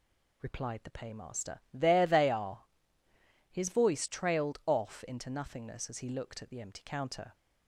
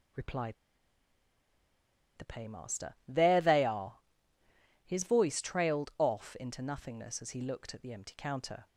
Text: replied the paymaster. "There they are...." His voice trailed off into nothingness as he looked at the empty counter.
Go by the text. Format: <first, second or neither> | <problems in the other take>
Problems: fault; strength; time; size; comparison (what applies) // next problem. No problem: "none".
first | pauses between "replied" and "the"; strong; at 0.5 s; 1.6 s long